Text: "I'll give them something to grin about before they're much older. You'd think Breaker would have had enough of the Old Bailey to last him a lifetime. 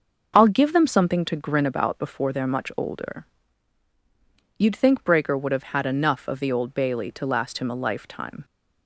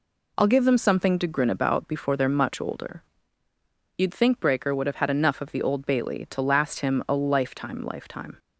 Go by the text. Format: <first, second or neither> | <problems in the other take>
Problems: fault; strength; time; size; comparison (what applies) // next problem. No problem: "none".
first | says "lifetime" twice; at 7.8 s